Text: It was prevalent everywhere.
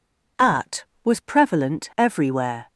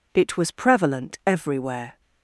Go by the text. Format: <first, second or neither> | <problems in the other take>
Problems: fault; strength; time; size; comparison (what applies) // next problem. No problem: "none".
second | says "At" for "It"; at 0.3 s